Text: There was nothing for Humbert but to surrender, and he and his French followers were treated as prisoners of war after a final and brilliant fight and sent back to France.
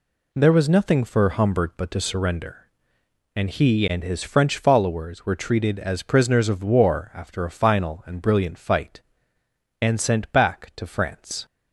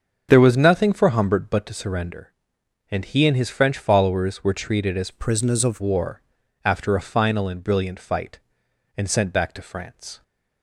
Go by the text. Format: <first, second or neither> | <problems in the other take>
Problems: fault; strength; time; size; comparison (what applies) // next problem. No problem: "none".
first | starts louder than the rest; until 1.3 s; 6.5 dB // changes voice from "prisoners" to "of"; from 5.1 to 5.8 s; 0.7 s long // pauses between "war" and "after"; at 6.2 s; 0.42 s long